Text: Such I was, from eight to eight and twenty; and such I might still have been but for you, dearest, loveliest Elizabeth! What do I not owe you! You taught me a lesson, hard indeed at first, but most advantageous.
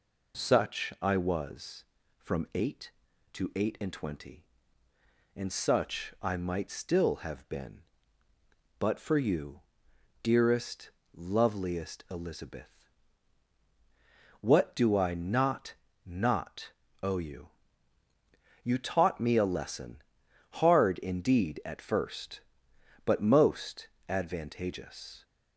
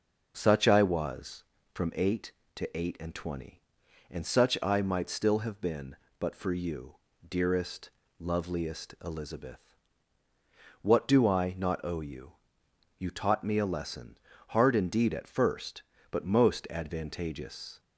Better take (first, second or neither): second